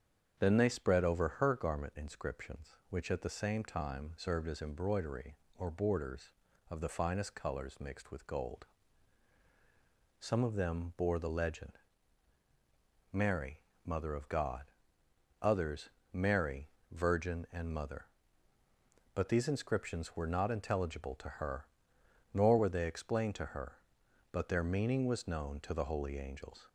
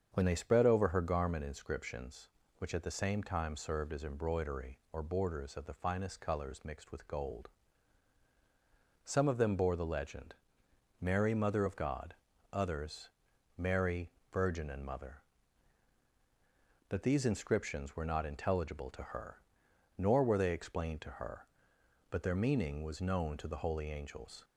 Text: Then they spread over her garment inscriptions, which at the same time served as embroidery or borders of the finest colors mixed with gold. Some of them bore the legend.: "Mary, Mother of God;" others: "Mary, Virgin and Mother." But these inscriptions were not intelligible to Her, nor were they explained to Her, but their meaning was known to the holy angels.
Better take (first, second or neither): first